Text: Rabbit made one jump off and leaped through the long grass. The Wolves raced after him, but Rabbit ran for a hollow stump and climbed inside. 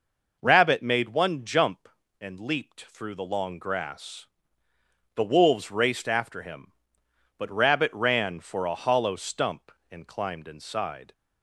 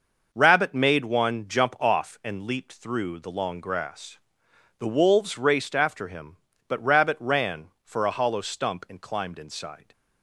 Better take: second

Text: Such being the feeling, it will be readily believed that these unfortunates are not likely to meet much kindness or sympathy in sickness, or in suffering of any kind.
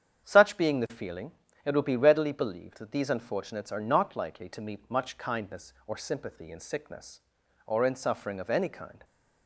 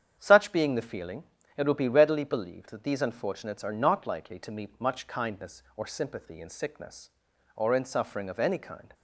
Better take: neither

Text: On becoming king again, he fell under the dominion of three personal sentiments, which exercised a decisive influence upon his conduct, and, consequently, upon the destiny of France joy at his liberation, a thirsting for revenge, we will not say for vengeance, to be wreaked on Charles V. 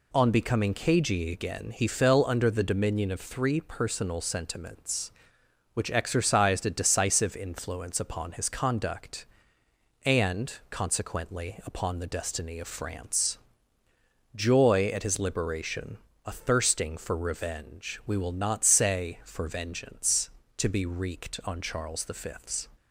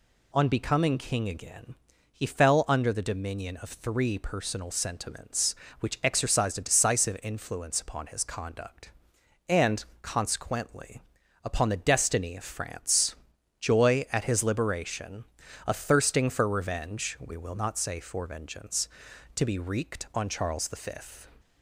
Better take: second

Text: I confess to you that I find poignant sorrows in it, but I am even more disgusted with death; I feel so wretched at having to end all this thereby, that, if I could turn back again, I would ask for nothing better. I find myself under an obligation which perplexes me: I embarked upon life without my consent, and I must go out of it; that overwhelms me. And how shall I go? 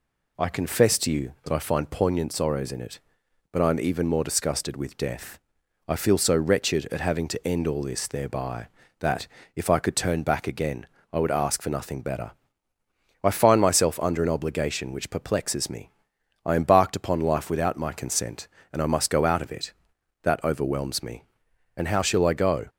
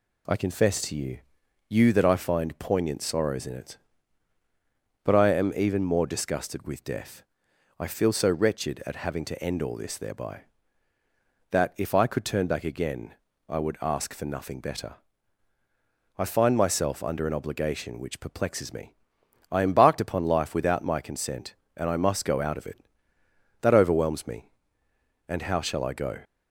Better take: first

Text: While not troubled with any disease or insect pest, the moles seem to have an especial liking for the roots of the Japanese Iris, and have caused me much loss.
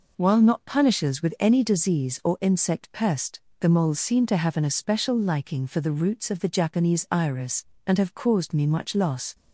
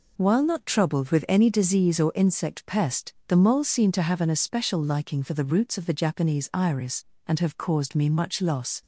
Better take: second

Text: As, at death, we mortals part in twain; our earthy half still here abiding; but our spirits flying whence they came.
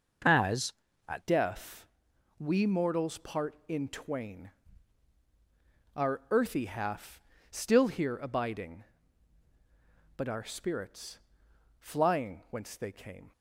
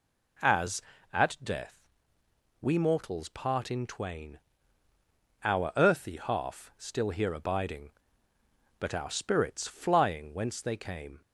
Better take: second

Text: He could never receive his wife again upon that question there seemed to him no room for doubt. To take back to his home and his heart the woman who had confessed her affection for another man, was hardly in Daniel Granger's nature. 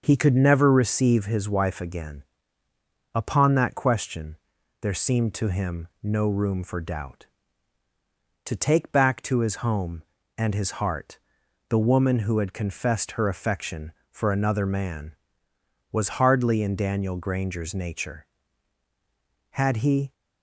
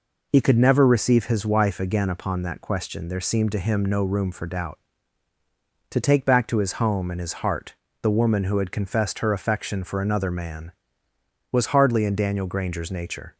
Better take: second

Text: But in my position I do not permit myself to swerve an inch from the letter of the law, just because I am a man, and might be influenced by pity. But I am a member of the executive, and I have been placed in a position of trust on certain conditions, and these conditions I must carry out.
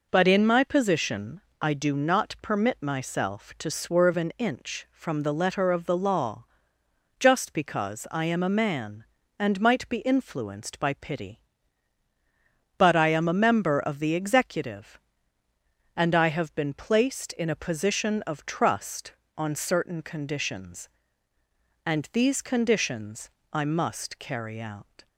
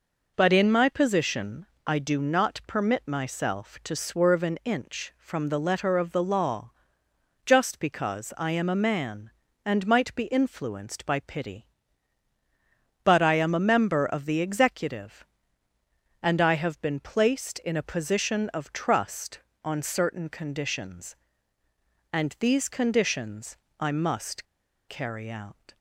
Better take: first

